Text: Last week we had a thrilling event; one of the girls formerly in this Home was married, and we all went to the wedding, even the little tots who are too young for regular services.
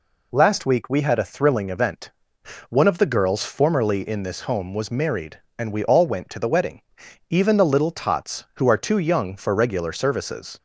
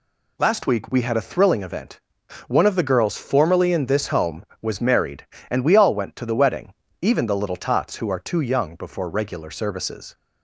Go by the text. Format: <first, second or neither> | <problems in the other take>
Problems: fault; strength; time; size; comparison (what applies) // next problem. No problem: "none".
first | says "before" for "for"; at 8.7 s